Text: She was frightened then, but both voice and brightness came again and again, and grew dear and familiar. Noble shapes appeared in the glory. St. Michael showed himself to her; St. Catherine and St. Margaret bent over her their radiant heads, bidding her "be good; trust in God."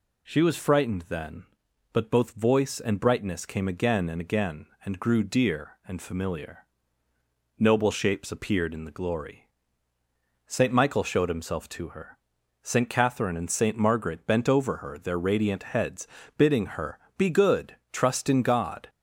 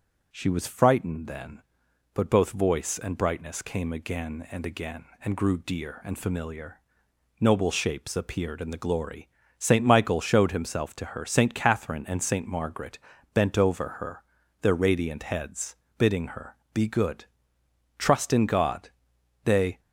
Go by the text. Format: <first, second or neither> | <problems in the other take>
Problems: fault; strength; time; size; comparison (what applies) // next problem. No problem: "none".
first | pauses between "Margaret" and "bent"; slight; at 12.9 s; 0.36 s long // pauses between "her" and "their"; at 14.2 s; 0.38 s long // pauses between "her" and "be"; slight; at 16.5 s; 0.16 s long; slight in the first // goes on to say "They"; slight; from 19.4 s on; 0.36 s long